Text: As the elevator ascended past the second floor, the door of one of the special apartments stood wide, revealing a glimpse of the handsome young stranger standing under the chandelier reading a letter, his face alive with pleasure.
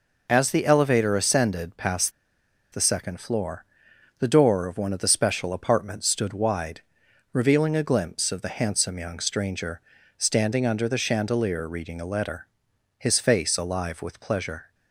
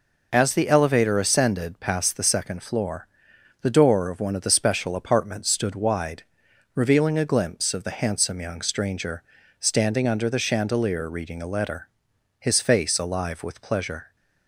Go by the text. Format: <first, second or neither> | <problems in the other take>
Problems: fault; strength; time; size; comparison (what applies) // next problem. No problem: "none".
second | pauses between "past" and "the"; noticeable; at 2.1 s; 0.62 s long // pauses between "stranger" and "standing"; at 9.8 s; 0.38 s long; also in the second